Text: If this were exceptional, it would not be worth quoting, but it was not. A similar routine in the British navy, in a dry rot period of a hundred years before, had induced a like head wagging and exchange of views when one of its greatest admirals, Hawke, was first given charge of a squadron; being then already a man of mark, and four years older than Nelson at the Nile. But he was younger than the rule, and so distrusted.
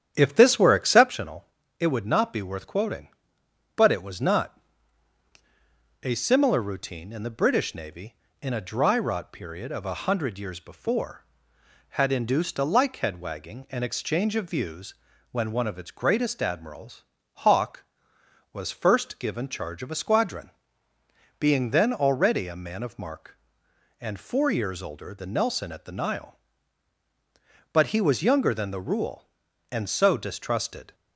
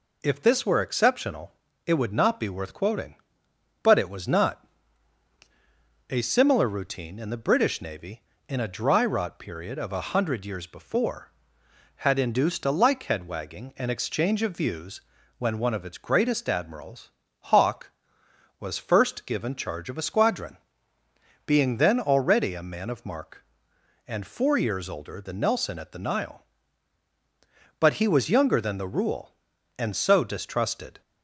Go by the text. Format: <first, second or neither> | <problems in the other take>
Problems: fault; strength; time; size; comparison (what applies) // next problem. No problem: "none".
second | starts louder than the rest; strong; until 1.2 s; 9.5 dB // pauses between "views" and "when"; at 14.9 s; 0.38 s long; also in the second